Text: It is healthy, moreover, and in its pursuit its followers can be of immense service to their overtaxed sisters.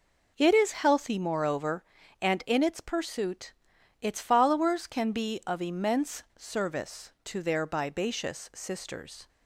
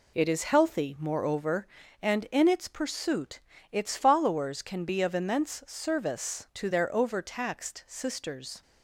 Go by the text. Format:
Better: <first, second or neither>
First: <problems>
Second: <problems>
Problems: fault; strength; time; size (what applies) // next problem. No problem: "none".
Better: second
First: pauses between "pursuit" and "its"; noticeable; at 3.5 s; 0.50 s long // says "bibacious" for "overtaxed"; at 7.6 s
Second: pauses between "pursuit" and "its"; slight; at 3.4 s; 0.32 s long